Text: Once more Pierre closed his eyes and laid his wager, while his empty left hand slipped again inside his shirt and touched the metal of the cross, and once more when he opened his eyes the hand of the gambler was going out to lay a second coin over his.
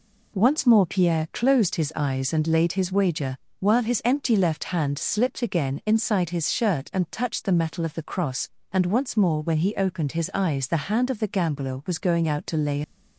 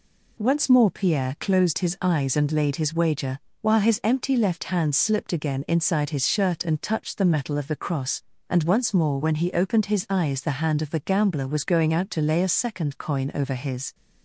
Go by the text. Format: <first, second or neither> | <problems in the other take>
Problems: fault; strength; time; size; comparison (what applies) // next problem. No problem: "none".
second | stops before "a second coin over his"; at 12.8 s